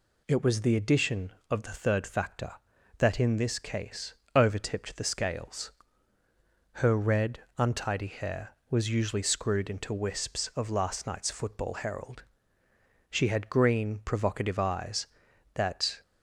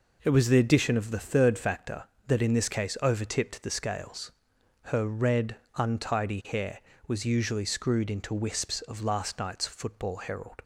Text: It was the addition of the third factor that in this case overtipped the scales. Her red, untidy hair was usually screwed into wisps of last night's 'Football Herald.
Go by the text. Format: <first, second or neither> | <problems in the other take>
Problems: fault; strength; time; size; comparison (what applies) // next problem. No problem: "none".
second | pauses between "case" and "overtipped"; slight; at 4.1 s; 0.20 s long // goes on to say "She had green provocative eyes that"; strong; from 13.0 s on; 2.9 s long